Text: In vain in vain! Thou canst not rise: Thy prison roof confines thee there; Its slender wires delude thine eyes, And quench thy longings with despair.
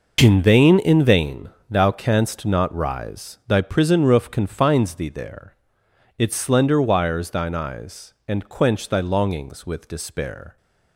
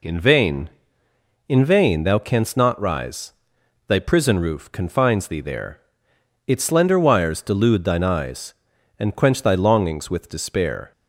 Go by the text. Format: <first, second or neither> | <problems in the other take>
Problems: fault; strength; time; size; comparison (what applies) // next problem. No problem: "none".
second | skips "delude"; at 7.3 s